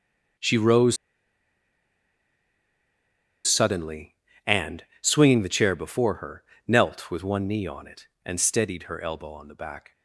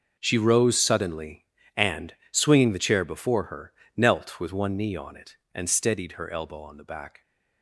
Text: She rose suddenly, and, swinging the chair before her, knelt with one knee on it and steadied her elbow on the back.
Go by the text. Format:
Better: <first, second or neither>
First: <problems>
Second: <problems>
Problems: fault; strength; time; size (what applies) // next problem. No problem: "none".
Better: second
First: pauses between "rose" and "suddenly"; strong; at 0.9 s; 2.5 s long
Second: none